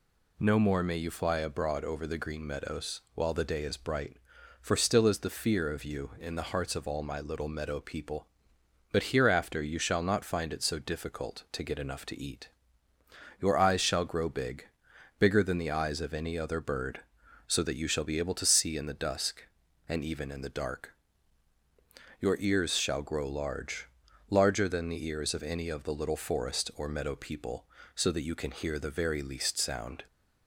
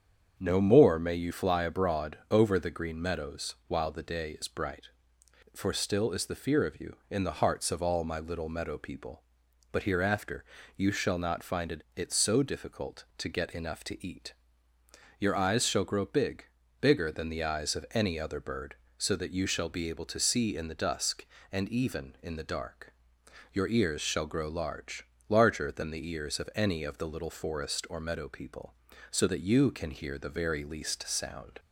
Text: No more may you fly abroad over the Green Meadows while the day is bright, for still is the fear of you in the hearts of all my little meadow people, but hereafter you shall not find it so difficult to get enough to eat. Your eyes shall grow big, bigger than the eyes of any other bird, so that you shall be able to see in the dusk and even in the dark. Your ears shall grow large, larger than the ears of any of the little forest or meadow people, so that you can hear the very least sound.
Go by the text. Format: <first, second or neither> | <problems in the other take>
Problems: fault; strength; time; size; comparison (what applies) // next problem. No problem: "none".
first | starts louder than the rest; strong; until 1.3 s; 7.5 dB // pauses between "hereafter" and "you"; slight; at 10.4 s; 0.32 s long // says "it" twice; at 11.9 s